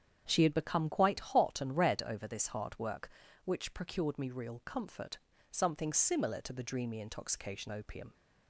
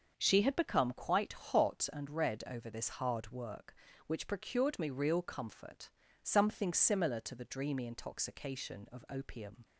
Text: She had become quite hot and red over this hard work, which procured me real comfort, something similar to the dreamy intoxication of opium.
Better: second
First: starts louder than the rest; strong; until 1.2 s; 8.5 dB // skips "of"; at 7.6 s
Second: starts louder than the rest; until 1.1 s; 6.5 dB

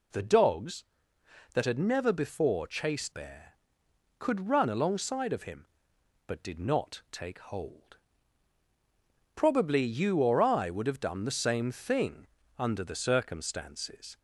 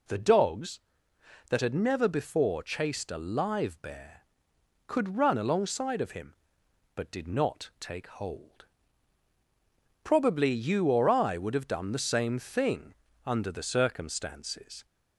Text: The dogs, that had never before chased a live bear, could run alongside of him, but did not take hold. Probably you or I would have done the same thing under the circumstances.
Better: second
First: skips "a live"; at 3.1 s // pauses between "thing" and "under"; slight; at 12.2 s; 0.32 s long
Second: pauses between "thing" and "under"; slight; at 12.9 s; 0.32 s long

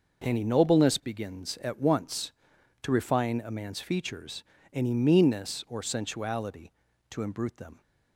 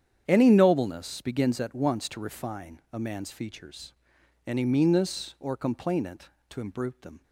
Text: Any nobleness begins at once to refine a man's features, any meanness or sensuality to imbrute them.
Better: first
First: none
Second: starts louder than the rest; strong; until 1.3 s; 9 dB // says "complainant" for "sensuality"; at 5.5 s

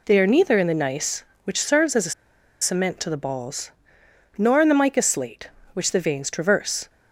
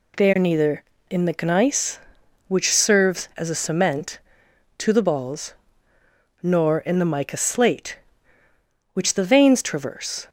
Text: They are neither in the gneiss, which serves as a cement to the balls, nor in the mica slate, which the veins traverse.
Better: second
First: pauses between "a" and "cement"; noticeable; at 2.1 s; 0.49 s long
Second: none

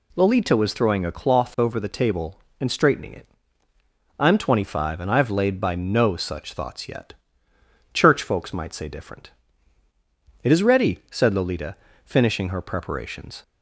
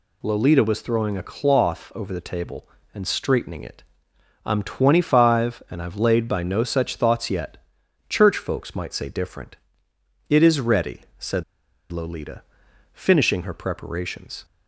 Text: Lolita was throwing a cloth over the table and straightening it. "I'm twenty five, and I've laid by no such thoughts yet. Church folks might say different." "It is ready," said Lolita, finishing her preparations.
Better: first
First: none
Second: pauses between "said" and "Lolita"; noticeable; at 11.4 s; 0.49 s long

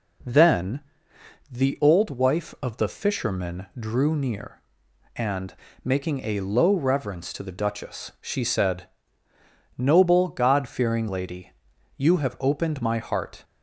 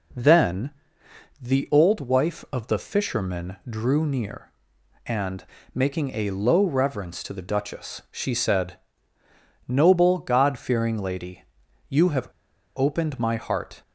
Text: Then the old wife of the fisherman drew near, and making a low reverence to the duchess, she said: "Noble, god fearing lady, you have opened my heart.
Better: first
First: pauses between "Then" and "the"; noticeable; at 0.8 s; 0.70 s long // pauses between "and" and "making"; slight; at 5.5 s; 0.28 s long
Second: pauses between "Then" and "the"; noticeable; at 0.7 s; 0.70 s long // pauses between "and" and "making"; slight; at 5.4 s; 0.28 s long // pauses between "have" and "opened"; noticeable; at 12.2 s; 0.50 s long

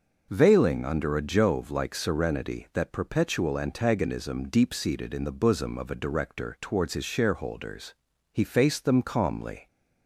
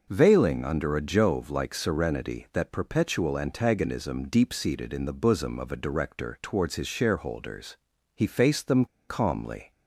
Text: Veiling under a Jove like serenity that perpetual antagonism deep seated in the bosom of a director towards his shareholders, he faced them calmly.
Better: first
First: none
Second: pauses between "them" and "calmly"; slight; at 8.8 s; 0.22 s long

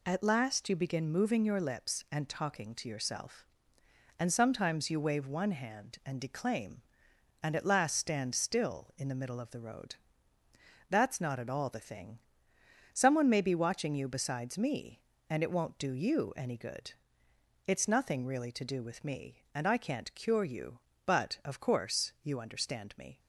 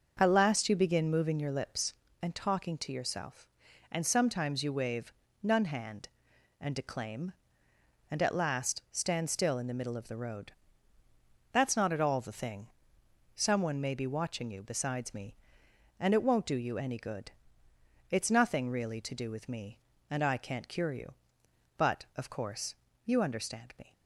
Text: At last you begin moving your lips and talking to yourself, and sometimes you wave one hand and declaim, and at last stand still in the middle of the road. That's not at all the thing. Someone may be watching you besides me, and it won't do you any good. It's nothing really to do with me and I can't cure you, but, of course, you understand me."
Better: first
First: none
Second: says "none" for "one"; at 5.4 s

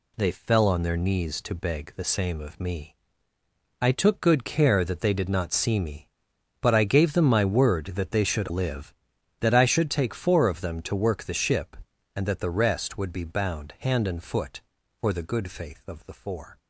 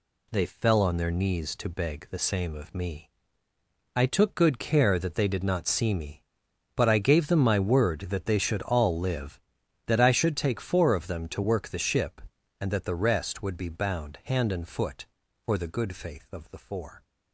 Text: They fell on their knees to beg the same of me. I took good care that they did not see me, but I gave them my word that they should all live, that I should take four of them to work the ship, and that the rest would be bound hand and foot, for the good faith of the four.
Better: second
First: skips "all"; at 8.5 s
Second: none

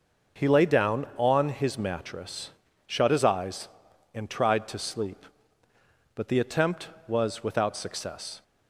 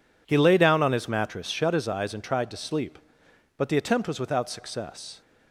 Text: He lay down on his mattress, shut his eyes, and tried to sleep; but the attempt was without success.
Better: neither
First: none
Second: none

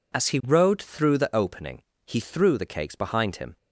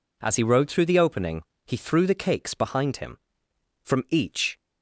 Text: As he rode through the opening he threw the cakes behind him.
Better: first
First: pauses between "opening" and "he"; slight; at 1.8 s; 0.26 s long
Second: pauses between "opening" and "he"; slight; at 1.4 s; 0.23 s long // goes on to say "From each"; noticeable; from 3.8 s on; 0.74 s long

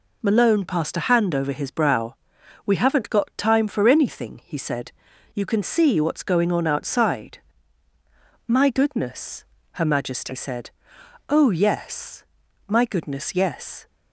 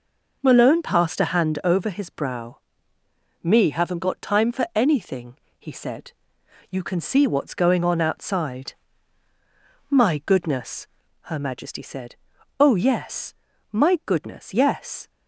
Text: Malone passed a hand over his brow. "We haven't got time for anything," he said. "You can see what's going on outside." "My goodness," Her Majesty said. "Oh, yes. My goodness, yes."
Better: first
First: none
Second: says "Me" for "We"; at 3.4 s

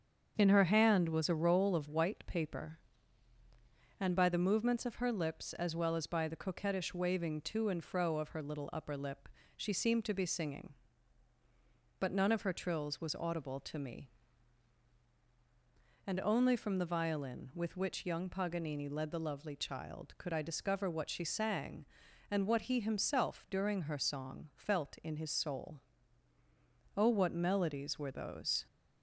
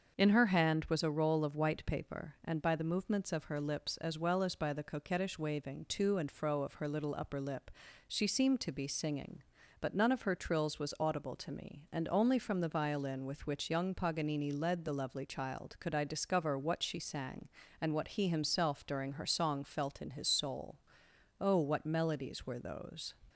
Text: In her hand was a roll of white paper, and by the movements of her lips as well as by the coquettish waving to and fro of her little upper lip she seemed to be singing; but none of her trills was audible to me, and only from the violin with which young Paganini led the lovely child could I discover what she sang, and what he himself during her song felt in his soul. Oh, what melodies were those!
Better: neither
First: starts louder than the rest; strong; until 1.3 s; 7.5 dB // pauses between "lip" and "she"; slight; at 9.3 s; 0.26 s long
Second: starts louder than the rest; until 1.2 s; 6.5 dB // pauses between "lip" and "she"; slight; at 7.7 s; 0.34 s long

